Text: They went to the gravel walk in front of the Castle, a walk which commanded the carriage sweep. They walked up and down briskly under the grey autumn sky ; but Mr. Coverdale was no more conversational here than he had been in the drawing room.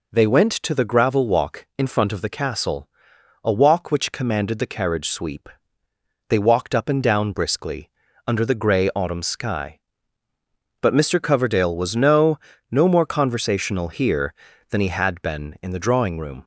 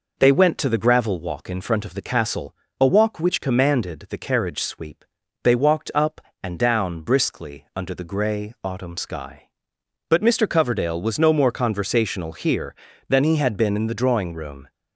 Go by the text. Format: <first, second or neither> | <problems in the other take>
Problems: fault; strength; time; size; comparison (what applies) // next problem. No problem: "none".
second | pauses between "briskly" and "under"; at 7.8 s; 0.40 s long // says "no" twice; at 12.6 s